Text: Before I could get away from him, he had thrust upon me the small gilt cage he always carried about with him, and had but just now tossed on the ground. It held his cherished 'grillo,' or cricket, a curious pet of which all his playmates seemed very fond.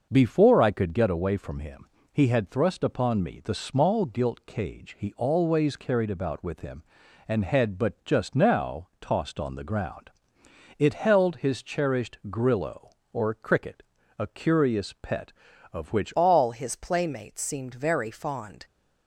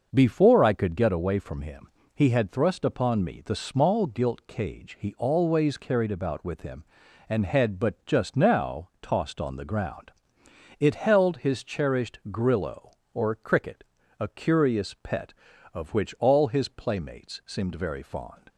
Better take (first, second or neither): second